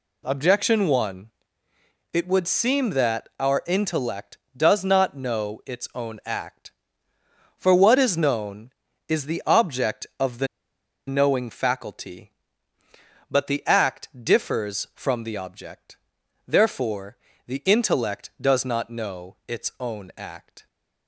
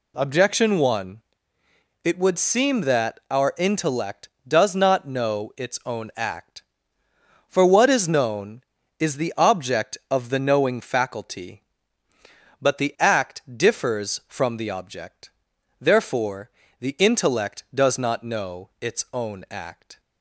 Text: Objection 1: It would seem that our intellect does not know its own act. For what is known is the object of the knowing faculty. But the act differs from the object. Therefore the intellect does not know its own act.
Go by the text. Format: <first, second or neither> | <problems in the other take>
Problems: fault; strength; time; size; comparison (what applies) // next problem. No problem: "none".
second | pauses between "the" and "knowing"; noticeable; at 10.4 s; 0.61 s long // pauses between "Therefore" and "the"; slight; at 17.1 s; 0.30 s long; slight in the second